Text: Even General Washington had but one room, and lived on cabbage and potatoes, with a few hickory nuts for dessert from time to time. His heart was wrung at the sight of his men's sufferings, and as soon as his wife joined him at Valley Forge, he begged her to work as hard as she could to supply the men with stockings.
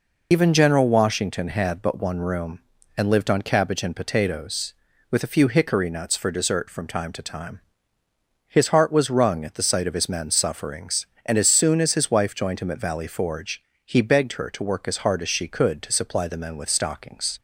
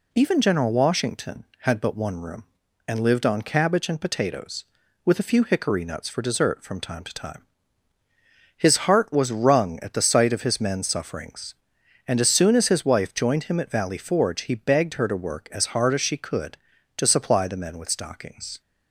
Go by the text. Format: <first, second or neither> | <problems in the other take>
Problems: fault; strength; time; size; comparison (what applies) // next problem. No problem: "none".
second | loses the start of "Even"; at 0.3 s; 100 ms